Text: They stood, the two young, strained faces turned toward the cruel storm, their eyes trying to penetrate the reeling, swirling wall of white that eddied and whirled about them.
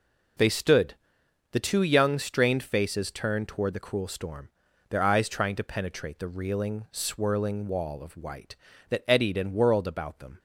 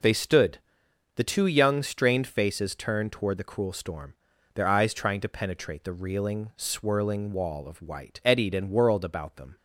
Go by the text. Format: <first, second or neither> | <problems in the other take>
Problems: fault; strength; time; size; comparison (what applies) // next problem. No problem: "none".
first | skips "that"; at 8.2 s